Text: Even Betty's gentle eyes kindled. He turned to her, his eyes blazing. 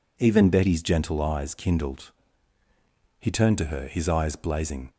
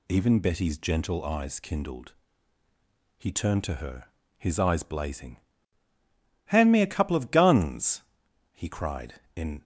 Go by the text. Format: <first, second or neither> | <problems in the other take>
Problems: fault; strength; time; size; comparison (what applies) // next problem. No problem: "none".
first | goes on to say "Hand me a couple of guns he cried in"; strong; from 6.4 s on; 3.1 s long